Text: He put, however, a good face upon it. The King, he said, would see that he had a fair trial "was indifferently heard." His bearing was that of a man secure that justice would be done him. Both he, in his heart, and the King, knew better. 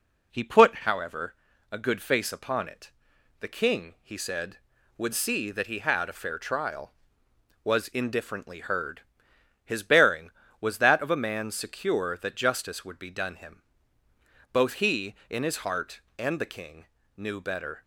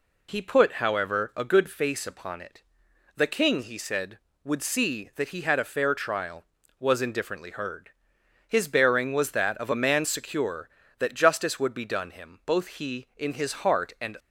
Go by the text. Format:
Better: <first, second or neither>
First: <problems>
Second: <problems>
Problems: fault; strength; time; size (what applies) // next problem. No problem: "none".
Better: first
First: none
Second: stops before "the King knew better"; at 14.1 s